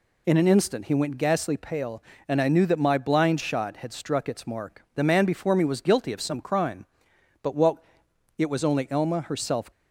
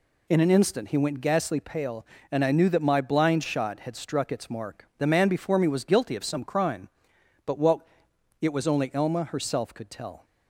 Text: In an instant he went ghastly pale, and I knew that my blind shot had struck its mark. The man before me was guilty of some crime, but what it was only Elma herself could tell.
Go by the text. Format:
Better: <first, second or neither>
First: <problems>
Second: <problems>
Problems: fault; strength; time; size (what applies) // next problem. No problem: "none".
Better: second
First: pauses between "what" and "it"; noticeable; at 7.7 s; 0.60 s long // stops before "could tell"; at 9.7 s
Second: pauses between "what" and "it"; noticeable; at 7.7 s; 0.60 s long